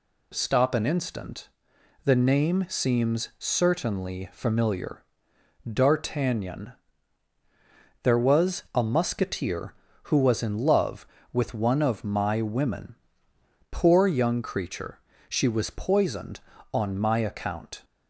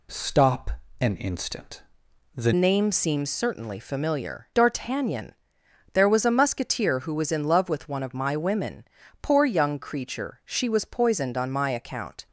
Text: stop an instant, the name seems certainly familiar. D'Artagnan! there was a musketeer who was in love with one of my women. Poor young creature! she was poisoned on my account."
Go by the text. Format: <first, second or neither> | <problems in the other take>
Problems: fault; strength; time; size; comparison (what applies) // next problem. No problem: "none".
first | pauses between "stop" and "an"; slight; at 0.7 s; 0.28 s long // changes voice at "name"; from 2.5 s on; 9.7 s long